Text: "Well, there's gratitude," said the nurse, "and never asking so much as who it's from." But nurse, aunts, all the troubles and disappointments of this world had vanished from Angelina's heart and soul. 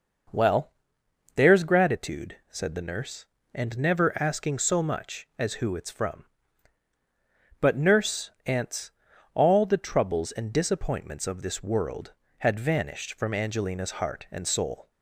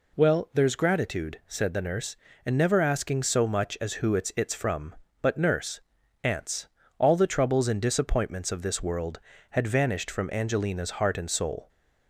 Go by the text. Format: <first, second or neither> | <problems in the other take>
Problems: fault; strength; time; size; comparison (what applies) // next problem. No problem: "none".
first | says "it's" twice; at 4.3 s